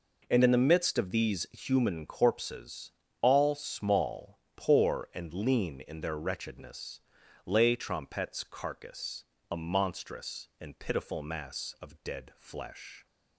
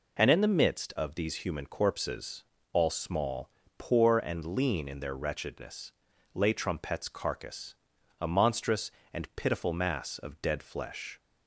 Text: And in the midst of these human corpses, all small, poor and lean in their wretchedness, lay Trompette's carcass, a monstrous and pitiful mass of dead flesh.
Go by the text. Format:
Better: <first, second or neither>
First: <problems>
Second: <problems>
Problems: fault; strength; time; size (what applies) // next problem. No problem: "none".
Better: neither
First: none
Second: none